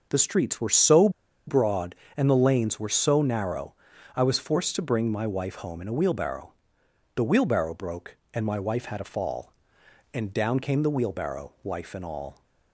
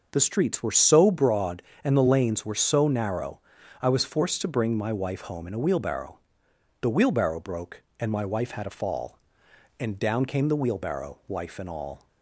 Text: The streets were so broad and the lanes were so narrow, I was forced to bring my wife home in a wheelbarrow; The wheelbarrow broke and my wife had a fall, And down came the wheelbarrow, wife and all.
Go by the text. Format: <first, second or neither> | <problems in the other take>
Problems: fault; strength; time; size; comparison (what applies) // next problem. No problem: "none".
second | starts louder than the rest; noticeable; until 1.1 s; 6 dB; noticeable in the second // pauses between "so" and "broad"; at 1.0 s; 0.37 s long